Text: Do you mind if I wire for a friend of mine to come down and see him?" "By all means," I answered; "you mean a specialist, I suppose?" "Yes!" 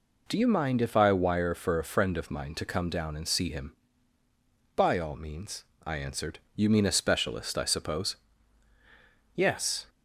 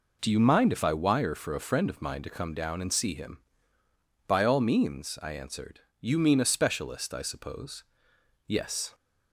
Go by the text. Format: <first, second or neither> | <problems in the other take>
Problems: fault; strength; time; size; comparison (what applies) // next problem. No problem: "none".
neither | none